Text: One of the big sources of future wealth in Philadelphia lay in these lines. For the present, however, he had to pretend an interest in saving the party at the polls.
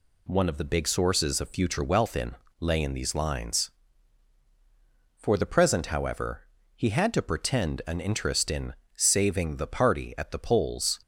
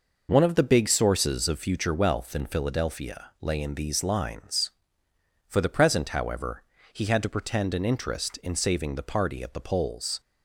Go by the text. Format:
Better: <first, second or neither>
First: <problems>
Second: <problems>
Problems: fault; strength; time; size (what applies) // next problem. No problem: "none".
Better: second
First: skips "Philadelphia"; at 2.4 s // pauses between "in" and "saving"; slight; at 8.7 s; 0.24 s long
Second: none